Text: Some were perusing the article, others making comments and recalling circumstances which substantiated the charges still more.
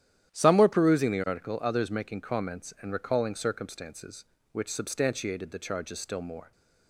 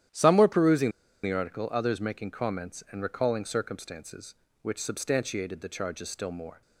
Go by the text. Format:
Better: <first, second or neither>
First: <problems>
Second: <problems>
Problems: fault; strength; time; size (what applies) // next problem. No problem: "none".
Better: first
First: starts louder than the rest; strong; until 1.3 s; 11 dB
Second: starts louder than the rest; strong; until 1.4 s; 11 dB // pauses between "perusing" and "the"; slight; at 0.9 s; 0.32 s long